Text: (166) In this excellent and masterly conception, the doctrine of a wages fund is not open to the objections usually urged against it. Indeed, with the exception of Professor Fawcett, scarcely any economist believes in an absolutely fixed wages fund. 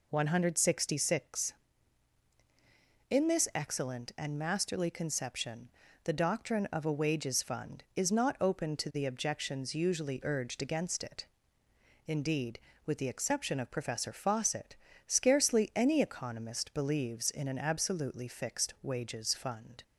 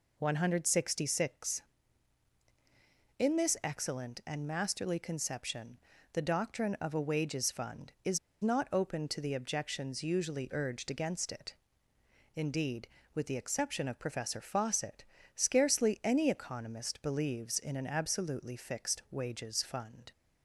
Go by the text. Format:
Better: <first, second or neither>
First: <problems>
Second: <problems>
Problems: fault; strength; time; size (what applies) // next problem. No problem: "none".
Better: first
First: none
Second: pauses between "is" and "not"; slight; at 8.1 s; 0.24 s long